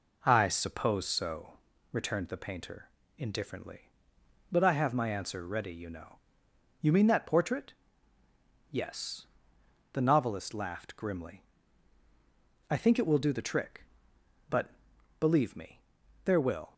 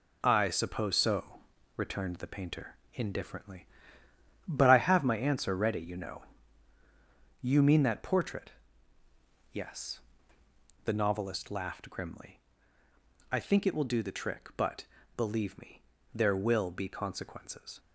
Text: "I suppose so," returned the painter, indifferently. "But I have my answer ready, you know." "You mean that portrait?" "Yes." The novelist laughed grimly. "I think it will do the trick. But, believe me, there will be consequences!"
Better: second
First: stops before "be consequences"; at 16.7 s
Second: none

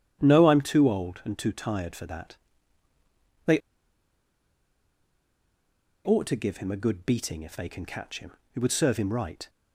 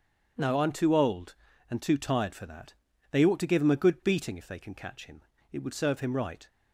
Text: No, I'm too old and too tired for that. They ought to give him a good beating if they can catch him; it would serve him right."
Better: second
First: starts louder than the rest; strong; until 1.2 s; 9.5 dB // pauses between "They" and "ought"; strong; at 3.5 s; 2.4 s long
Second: starts louder than the rest; strong; until 1.7 s; 8 dB

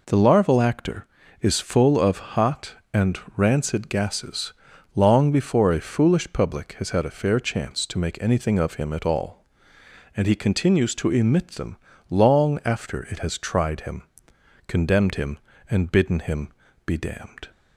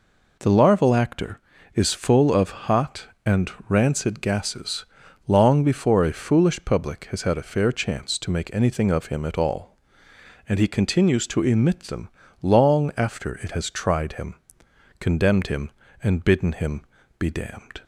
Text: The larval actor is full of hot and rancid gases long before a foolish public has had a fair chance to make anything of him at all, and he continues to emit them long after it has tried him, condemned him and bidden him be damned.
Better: neither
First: pauses between "and" and "rancid"; slight; at 3.1 s; 0.18 s long // pauses between "gases" and "long"; at 4.5 s; 0.42 s long // pauses between "them" and "long"; slight; at 11.7 s; 0.34 s long // pauses between "him" and "be"; slight; at 16.4 s; 0.36 s long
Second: pauses between "and" and "rancid"; slight; at 3.5 s; 0.18 s long // pauses between "gases" and "long"; at 4.8 s; 0.42 s long // pauses between "them" and "long"; slight; at 12.0 s; 0.34 s long // pauses between "him" and "be"; slight; at 16.8 s; 0.36 s long

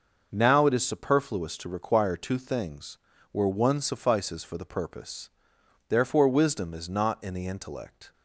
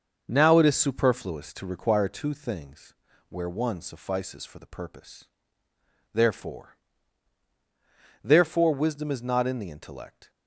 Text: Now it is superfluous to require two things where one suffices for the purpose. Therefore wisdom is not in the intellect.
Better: first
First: starts louder than the rest; noticeable; until 1.3 s; 6 dB // pauses between "things" and "where"; slight; at 2.9 s; 0.34 s long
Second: starts louder than the rest; until 1.2 s; 6.5 dB // pauses between "things" and "where"; slight; at 2.9 s; 0.34 s long // says "Therefore" twice; at 8.2 s

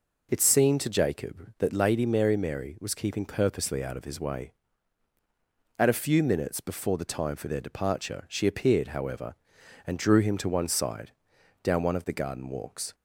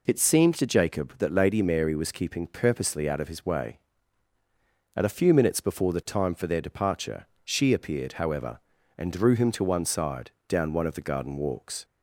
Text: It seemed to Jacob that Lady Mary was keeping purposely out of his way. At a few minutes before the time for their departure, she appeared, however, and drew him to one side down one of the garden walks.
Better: second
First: says "Mary" twice; at 2.3 s // pauses between "side" and "down"; noticeable; at 11.0 s; 0.54 s long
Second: pauses between "side" and "down"; slight; at 10.3 s; 0.18 s long

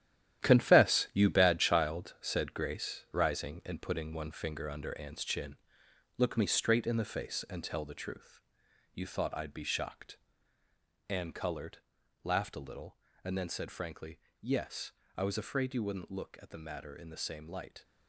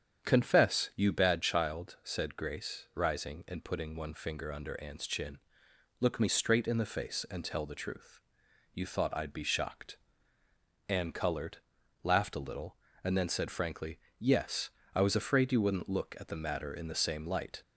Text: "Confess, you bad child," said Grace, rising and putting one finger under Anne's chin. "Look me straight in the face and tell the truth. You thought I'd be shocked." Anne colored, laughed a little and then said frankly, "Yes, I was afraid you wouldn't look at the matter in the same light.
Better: second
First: gets quieter; strong; throughout; 10.5 dB // starts louder than the rest; strong; until 1.4 s; 11.5 dB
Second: starts louder than the rest; strong; until 1.3 s; 8 dB

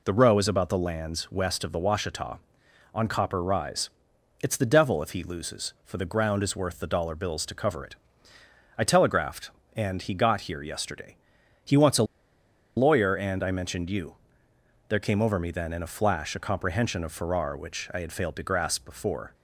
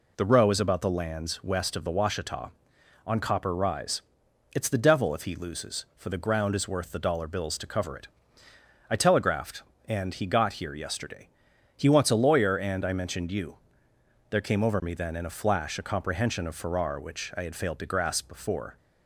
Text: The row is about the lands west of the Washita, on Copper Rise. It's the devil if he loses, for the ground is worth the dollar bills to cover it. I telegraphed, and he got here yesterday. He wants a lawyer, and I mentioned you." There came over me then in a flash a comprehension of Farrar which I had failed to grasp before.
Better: second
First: pauses between "a" and "lawyer"; noticeable; at 12.0 s; 0.73 s long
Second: none

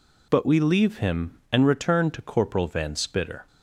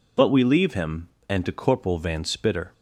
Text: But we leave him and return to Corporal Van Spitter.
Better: first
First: none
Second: skips "return"; at 1.4 s

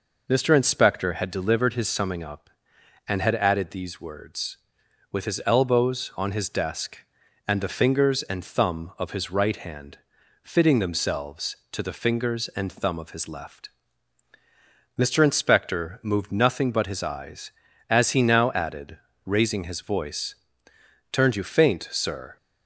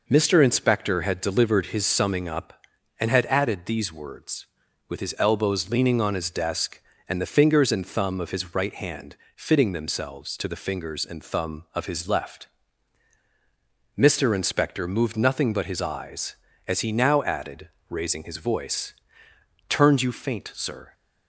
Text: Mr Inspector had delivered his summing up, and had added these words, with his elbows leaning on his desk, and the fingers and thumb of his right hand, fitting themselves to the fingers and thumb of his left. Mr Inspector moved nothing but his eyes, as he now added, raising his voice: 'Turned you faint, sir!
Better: second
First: skips "leaning"; at 6.1 s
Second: none

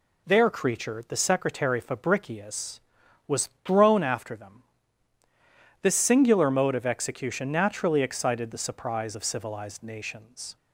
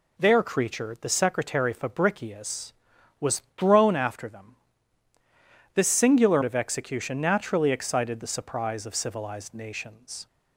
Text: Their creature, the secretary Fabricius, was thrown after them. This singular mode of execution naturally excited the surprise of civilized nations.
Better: first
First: none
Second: skips "mode"; at 6.4 s

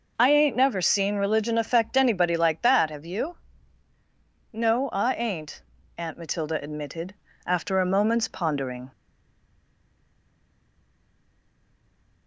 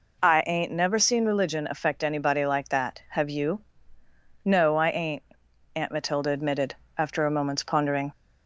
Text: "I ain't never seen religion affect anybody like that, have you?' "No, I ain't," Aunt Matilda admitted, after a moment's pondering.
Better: second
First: stays silent after the last word; strong; from 8.9 s on; 3.3 s long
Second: none

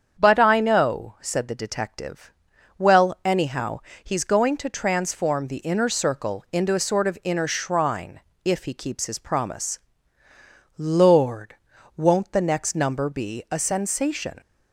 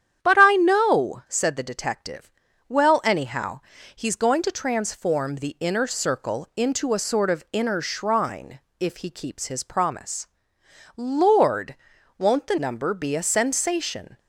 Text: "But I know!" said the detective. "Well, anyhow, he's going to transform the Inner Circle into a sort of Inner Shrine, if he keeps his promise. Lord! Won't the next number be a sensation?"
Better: first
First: starts louder than the rest; strong; until 1.2 s; 7.5 dB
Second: starts louder than the rest; strong; until 1.3 s; 9.5 dB // skips "next"; at 12.5 s

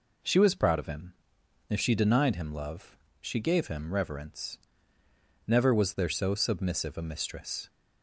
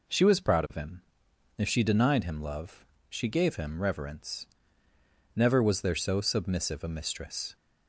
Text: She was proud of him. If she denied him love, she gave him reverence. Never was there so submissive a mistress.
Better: neither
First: none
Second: none

